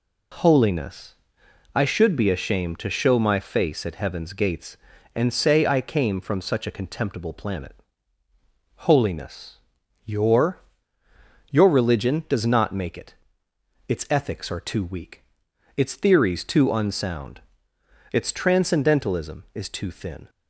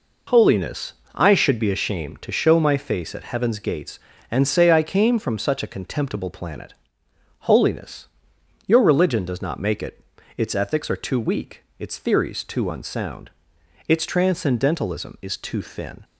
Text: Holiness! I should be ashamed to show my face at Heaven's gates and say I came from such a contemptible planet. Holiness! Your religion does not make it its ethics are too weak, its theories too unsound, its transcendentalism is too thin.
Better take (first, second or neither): second